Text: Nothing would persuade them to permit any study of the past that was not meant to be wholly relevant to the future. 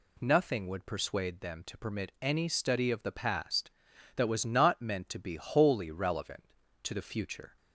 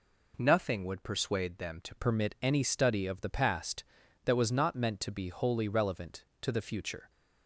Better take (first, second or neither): first